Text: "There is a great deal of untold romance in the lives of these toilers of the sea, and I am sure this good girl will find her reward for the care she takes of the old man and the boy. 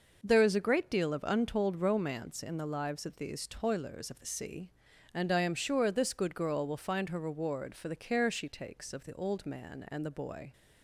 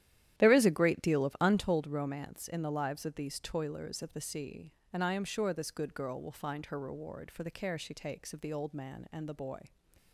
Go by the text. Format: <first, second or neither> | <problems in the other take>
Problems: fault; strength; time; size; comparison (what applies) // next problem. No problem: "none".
first | starts louder than the rest; strong; until 1.8 s; 11.5 dB